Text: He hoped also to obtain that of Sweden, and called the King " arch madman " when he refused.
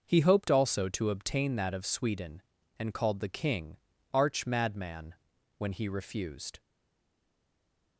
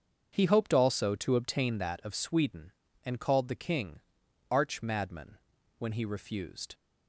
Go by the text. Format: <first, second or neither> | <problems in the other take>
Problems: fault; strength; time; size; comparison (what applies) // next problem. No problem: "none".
second | starts louder than the rest; until 1.0 s; 6.5 dB; strong in the second // stays silent after the last word; noticeable; from 6.5 s on; 1.4 s long